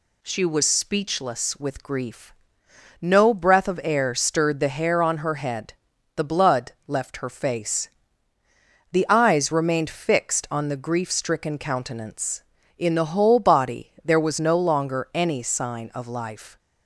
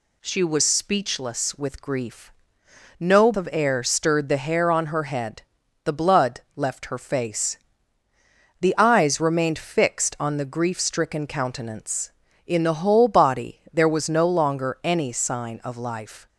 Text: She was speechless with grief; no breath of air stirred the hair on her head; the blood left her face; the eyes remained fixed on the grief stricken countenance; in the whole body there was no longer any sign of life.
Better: first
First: none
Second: skips "breath"; at 3.3 s

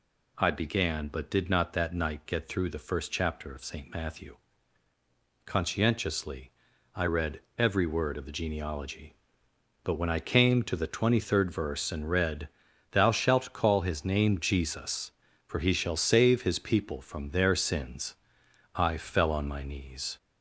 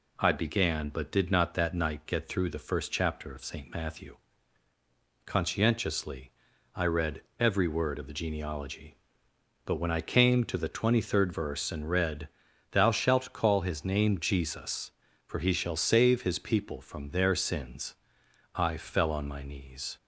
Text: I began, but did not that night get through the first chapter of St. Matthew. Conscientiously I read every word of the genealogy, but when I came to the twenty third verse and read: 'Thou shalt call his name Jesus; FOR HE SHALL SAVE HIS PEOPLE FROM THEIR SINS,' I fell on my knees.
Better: second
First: gets louder; slight; throughout; 3 dB // pauses between "Conscientiously" and "I"; at 6.5 s; 0.44 s long // pauses between "read" and "every"; slight; at 7.4 s; 0.18 s long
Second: pauses between "Conscientiously" and "I"; at 6.3 s; 0.44 s long // pauses between "read" and "every"; slight; at 7.2 s; 0.18 s long

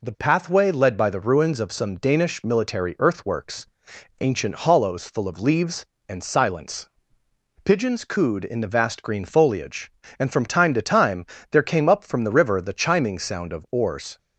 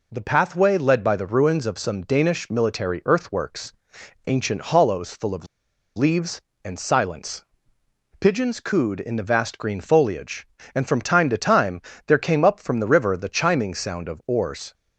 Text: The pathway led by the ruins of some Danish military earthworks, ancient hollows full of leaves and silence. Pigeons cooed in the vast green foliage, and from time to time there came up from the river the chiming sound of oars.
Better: first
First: pauses between "time" and "there"; slight; at 11.2 s; 0.26 s long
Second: pauses between "of" and "leaves"; noticeable; at 5.4 s; 0.50 s long // pauses between "time" and "there"; slight; at 11.8 s; 0.26 s long

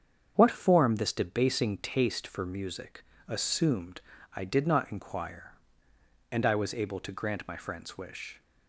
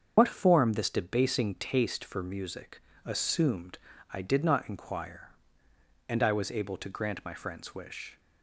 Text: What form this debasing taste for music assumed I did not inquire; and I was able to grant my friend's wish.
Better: first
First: starts louder than the rest; strong; until 1.3 s; 7.5 dB // pauses between "music" and "assumed"; slight; at 3.0 s; 0.20 s long // pauses between "assumed" and "I"; slight; at 4.0 s; 0.32 s long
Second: loses the start of "What"; at 0.1 s; 45 ms // starts louder than the rest; until 1.1 s; 7 dB // pauses between "music" and "assumed"; slight; at 2.8 s; 0.20 s long // pauses between "assumed" and "I"; slight; at 3.7 s; 0.32 s long

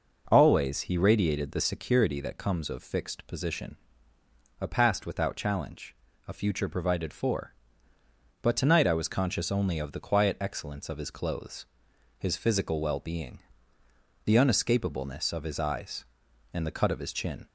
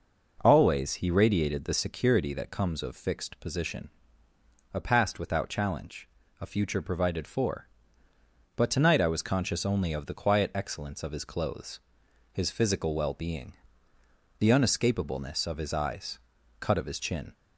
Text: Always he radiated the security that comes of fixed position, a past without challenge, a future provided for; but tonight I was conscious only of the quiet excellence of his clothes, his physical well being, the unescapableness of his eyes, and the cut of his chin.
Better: first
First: none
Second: skips "and the"; at 16.4 s

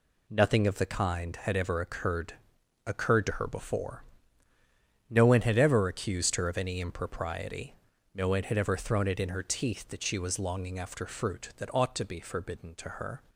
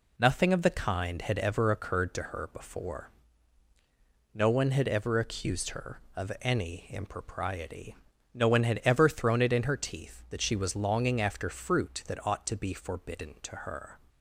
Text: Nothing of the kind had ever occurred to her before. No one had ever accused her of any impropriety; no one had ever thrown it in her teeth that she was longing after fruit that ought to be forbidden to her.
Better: second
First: says "occurred" twice; at 2.8 s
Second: none

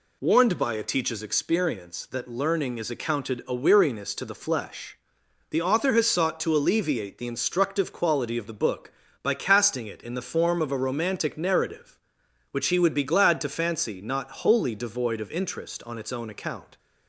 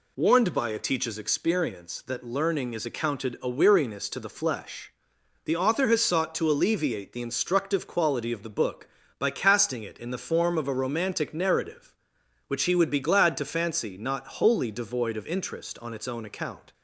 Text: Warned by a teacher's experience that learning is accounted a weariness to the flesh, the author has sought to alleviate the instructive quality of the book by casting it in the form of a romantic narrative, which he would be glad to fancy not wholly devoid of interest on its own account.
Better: neither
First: none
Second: none

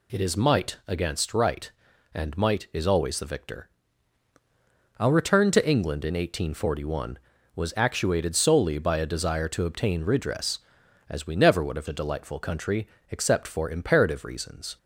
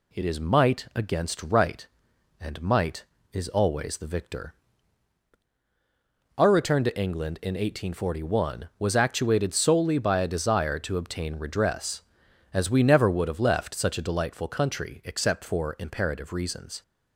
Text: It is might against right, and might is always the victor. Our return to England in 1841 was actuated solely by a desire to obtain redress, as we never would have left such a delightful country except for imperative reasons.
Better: second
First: skips "left such"; at 11.8 s // pauses between "country" and "except"; slight; at 12.8 s; 0.22 s long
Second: none

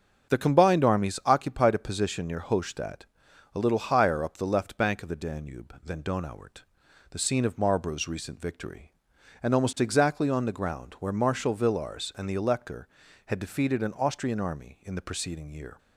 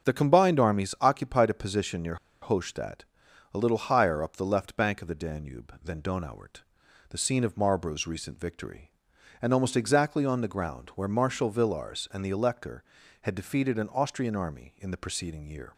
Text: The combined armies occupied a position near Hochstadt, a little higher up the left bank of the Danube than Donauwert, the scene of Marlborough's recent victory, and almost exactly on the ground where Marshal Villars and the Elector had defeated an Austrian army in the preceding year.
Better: first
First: starts louder than the rest; until 1.3 s; 7 dB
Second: starts louder than the rest; until 1.1 s; 7 dB // pauses between "near" and "Hochstadt"; slight; at 2.1 s; 0.26 s long

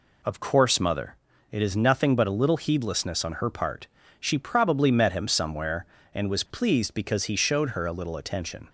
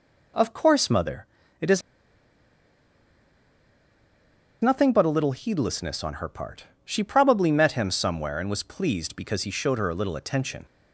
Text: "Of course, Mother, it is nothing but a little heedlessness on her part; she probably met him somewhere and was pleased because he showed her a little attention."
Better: first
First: none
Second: pauses between "is" and "nothing"; strong; at 1.8 s; 2.8 s long

